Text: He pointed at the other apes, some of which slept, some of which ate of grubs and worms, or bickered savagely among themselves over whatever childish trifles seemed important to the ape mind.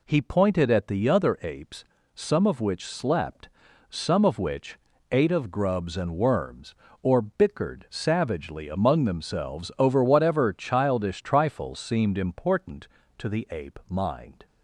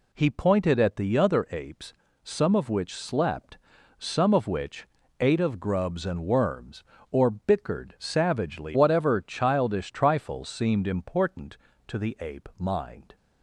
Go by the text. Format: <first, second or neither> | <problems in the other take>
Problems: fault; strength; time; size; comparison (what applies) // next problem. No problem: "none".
first | pauses between "which" and "ate"; slight; at 4.8 s; 0.34 s long; slight in the first // skips "among themselves over"; at 8.7 s